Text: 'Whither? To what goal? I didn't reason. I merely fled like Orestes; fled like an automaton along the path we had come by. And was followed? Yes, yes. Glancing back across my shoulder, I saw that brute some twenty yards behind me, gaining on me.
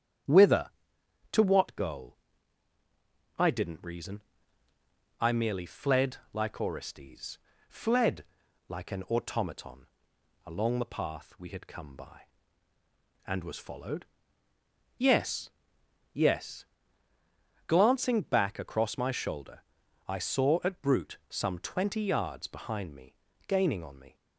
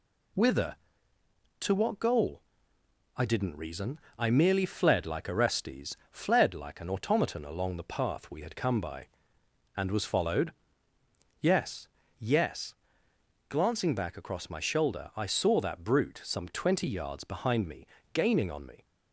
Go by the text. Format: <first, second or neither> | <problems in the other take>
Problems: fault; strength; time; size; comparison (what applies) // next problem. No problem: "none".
second | starts louder than the rest; strong; until 1.9 s; 9.5 dB // pauses between "fled" and "like"; slight; at 6.1 s; 0.16 s long // pauses between "fled" and "like"; at 8.2 s; 0.44 s long // pauses between "automaton" and "along"; noticeable; at 9.8 s; 0.58 s long // says "at" for "that"; at 20.6 s